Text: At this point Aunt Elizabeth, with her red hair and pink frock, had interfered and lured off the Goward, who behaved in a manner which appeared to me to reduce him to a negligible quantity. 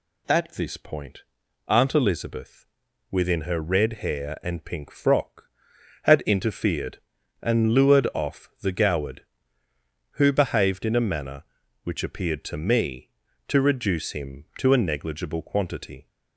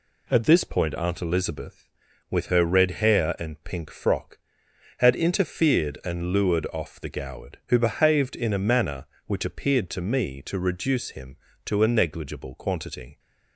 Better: second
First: pauses between "point" and "Aunt"; noticeable; at 1.2 s; 0.46 s long // says "within" for "with"; at 3.1 s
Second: none

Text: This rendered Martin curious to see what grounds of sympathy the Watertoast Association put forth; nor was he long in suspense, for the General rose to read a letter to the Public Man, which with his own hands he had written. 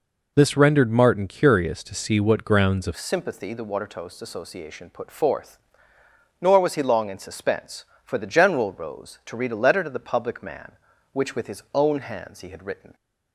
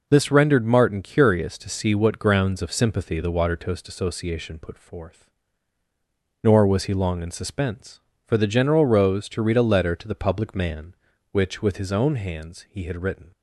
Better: second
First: changes voice at "sympathy"; from 2.9 s on; 10.0 s long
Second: none

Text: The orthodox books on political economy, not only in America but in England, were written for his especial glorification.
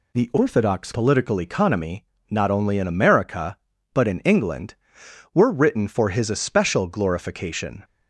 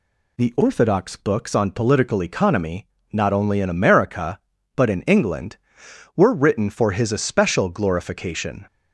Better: second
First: skips "books on"; at 0.9 s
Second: none

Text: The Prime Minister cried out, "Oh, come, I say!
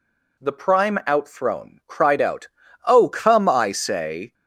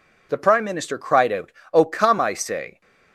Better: second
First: says "Outthrown" for "Minister"; at 1.0 s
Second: none

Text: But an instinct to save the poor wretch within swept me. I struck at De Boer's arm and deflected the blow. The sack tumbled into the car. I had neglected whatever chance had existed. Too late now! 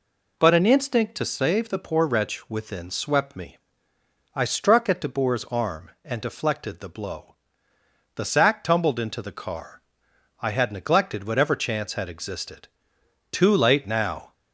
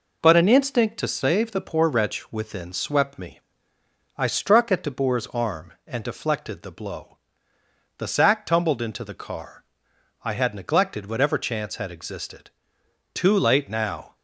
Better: first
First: none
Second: gets quieter; slight; throughout; 2.5 dB

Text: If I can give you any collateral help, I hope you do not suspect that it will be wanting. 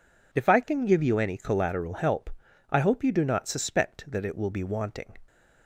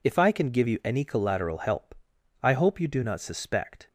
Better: first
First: none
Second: stops before "that it will be wanting"; at 3.8 s

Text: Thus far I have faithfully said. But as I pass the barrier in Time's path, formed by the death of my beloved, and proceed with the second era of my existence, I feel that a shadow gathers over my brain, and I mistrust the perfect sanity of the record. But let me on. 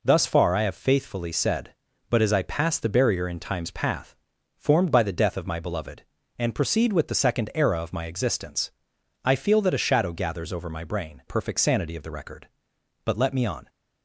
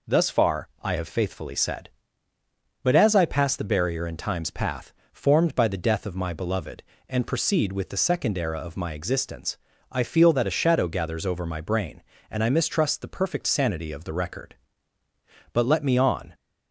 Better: second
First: skips "and I mistrust the"; at 11.2 s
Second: none

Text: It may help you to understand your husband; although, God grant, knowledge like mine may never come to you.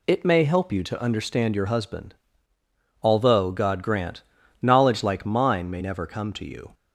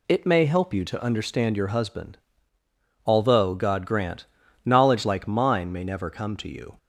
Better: neither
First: none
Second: none

